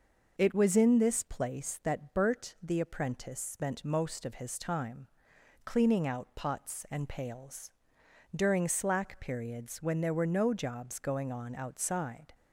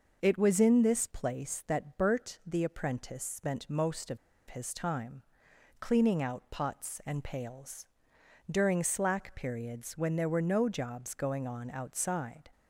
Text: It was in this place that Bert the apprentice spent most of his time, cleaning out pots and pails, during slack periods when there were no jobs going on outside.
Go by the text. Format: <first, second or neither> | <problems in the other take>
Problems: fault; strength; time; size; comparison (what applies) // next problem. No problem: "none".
first | pauses between "of" and "his"; slight; at 4.1 s; 0.32 s long